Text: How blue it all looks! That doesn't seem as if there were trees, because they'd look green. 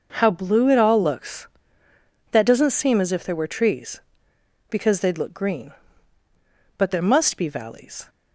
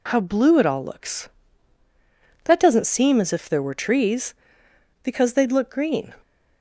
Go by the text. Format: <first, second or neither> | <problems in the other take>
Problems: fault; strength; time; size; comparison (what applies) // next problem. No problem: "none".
second | goes on to say "But there must be valleys"; noticeable; from 6.7 s on; 1.3 s long